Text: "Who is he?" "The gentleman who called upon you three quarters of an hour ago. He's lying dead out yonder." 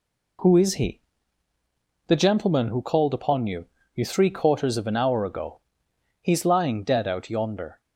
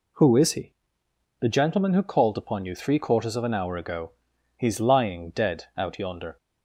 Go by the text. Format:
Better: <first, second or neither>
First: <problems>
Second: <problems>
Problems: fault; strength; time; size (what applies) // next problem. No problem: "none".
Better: second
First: says "you" twice; at 3.9 s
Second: none